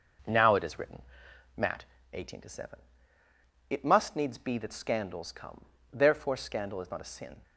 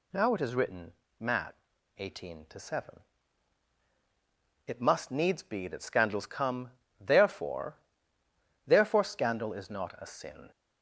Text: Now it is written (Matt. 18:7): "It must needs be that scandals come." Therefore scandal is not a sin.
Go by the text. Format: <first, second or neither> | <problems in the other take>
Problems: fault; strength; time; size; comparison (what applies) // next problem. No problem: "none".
first | says "Therefore" twice; at 8.6 s